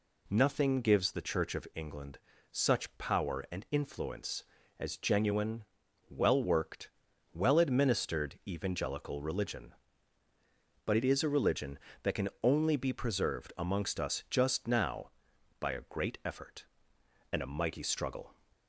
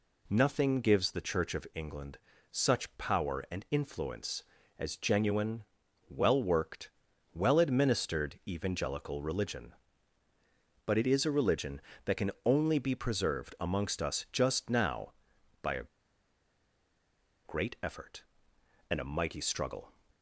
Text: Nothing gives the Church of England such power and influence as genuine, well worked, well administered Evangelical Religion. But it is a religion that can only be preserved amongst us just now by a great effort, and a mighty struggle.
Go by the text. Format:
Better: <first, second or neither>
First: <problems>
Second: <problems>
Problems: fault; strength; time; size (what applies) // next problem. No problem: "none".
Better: first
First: pauses between "England" and "such"; slight; at 2.1 s; 0.32 s long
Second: pauses between "England" and "such"; slight; at 2.1 s; 0.32 s long // pauses between "a" and "great"; strong; at 15.8 s; 1.6 s long